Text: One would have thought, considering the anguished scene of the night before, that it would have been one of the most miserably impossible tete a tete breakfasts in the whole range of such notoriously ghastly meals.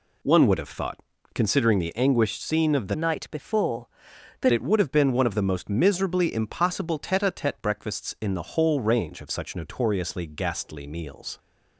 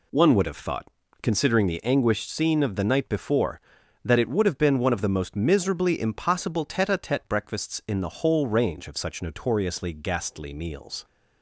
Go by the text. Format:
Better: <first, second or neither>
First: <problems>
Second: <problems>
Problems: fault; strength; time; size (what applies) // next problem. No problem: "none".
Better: second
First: changes voice from "night" to "that"; from 2.9 to 4.5 s; 1.6 s long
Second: none